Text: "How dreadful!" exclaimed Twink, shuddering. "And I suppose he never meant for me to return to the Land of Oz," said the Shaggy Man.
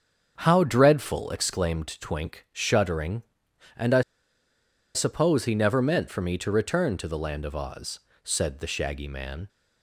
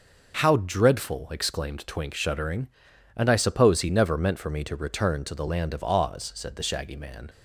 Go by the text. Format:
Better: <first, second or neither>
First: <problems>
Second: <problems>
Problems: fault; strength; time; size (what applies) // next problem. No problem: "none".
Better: second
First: starts louder than the rest; until 1.4 s; 7 dB // pauses between "I" and "suppose"; noticeable; at 4.0 s; 0.92 s long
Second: none